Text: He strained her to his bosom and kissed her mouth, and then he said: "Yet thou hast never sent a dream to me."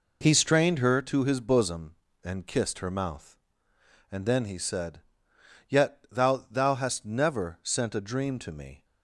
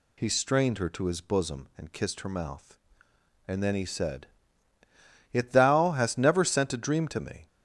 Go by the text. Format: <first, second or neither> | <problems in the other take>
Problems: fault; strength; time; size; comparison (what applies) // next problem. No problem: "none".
second | says "thou" twice; at 6.4 s